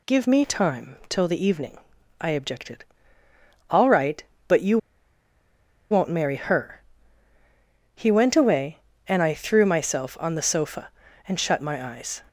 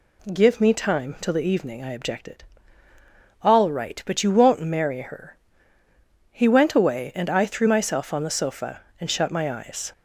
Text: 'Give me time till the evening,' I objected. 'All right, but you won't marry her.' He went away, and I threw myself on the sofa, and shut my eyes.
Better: second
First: pauses between "you" and "won't"; at 4.7 s; 1.1 s long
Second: none

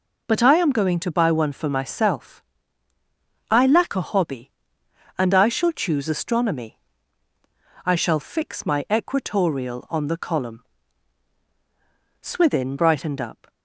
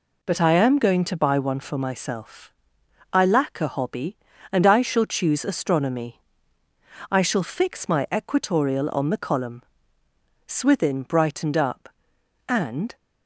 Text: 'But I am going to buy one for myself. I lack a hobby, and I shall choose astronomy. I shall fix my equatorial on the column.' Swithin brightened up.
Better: first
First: none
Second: goes on to say "And"; slight; from 12.4 s on; 0.48 s long

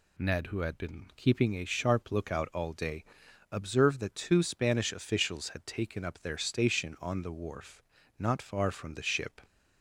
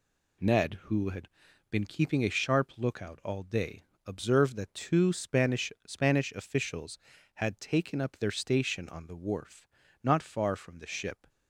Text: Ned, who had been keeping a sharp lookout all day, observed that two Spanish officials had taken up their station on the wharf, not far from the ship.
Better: first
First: none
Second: pauses between "had" and "been"; at 1.2 s; 0.42 s long // says "Spanish" twice; at 5.8 s

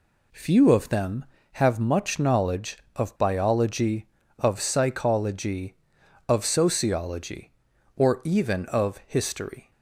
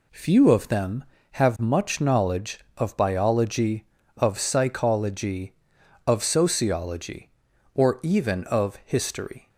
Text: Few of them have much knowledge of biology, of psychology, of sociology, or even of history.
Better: neither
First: none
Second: none

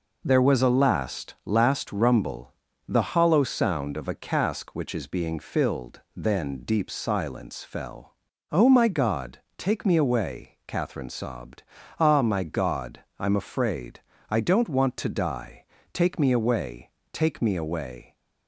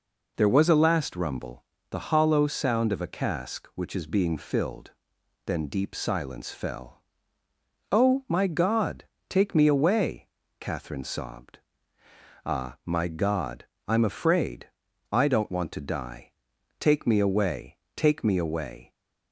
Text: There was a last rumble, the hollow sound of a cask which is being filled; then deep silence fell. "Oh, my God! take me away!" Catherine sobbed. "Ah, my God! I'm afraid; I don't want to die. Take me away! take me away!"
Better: second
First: says "last" twice; at 1.4 s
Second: none

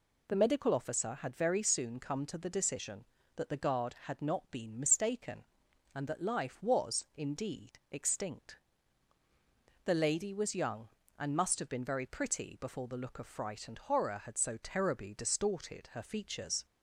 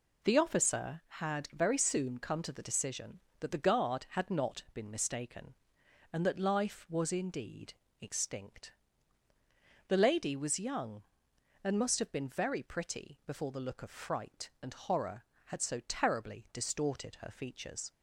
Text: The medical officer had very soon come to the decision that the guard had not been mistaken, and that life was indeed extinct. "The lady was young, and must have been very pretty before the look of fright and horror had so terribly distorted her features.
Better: first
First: none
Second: skips "medical"; at 0.3 s // pauses between "indeed" and "extinct"; slight; at 7.7 s; 0.30 s long

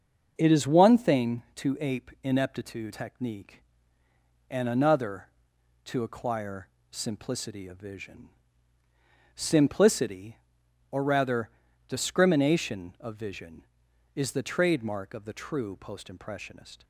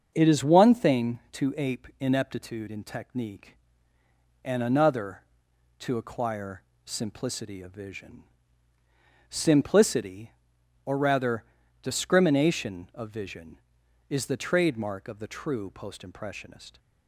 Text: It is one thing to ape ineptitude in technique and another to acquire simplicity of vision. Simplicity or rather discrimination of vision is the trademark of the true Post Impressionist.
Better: second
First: starts louder than the rest; until 1.3 s; 6.5 dB // skips "in"; at 2.9 s // pauses between "acquire" and "simplicity"; slight; at 6.6 s; 0.22 s long // pauses between "rather" and "discrimination"; at 11.4 s; 0.38 s long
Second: starts louder than the rest; until 1.1 s; 7 dB // pauses between "acquire" and "simplicity"; slight; at 6.6 s; 0.22 s long // pauses between "rather" and "discrimination"; at 11.4 s; 0.38 s long

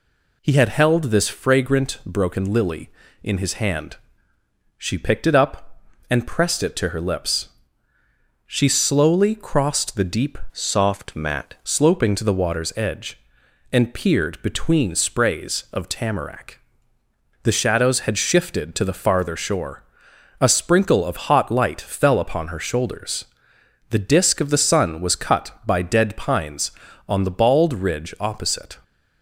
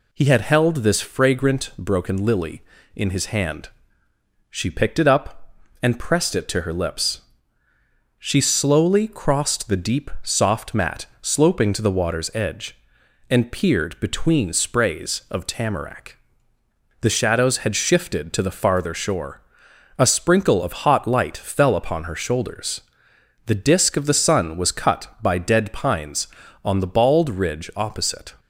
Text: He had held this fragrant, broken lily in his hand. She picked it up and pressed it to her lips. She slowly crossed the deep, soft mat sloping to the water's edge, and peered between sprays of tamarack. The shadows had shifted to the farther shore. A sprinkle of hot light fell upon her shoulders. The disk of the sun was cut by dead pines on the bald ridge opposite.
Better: second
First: changes voice from "soft" to "mat"; from 10.5 to 11.5 s; 1.0 s long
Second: none

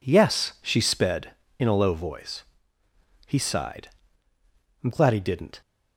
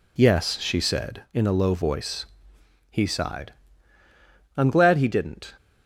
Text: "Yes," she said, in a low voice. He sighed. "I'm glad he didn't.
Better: second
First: says "sped" for "said"; at 0.8 s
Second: none

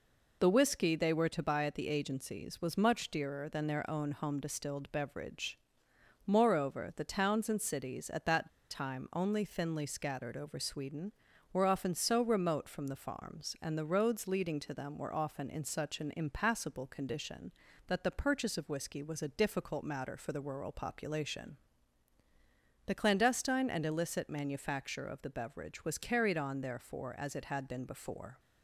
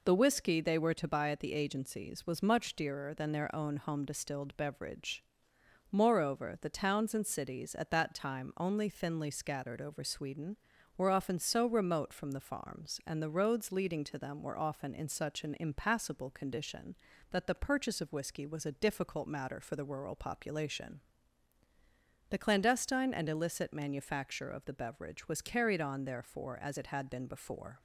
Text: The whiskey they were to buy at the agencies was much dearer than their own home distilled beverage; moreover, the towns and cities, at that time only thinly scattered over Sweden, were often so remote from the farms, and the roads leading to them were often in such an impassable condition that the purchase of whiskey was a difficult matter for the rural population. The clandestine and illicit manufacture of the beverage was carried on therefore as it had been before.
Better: second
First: pauses between "that" and "time"; slight; at 8.4 s; 0.22 s long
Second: none

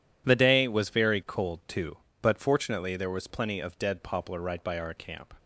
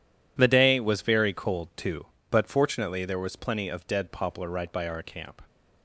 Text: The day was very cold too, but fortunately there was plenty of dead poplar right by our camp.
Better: neither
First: none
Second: none

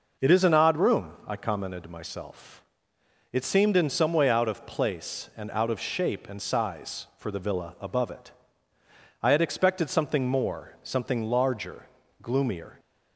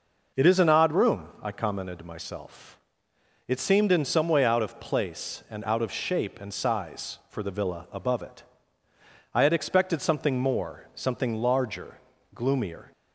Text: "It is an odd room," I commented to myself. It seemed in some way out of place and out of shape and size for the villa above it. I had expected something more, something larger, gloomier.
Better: neither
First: none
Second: none

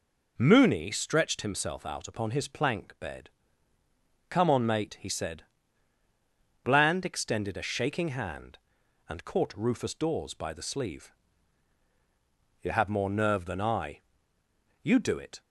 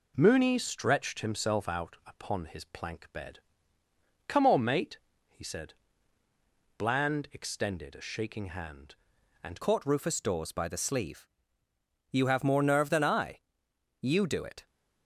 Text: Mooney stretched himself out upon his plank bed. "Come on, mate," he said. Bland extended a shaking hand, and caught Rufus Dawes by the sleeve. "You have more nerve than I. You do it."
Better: first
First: none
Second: changes voice at "caught"; from 9.6 s on; 5.0 s long

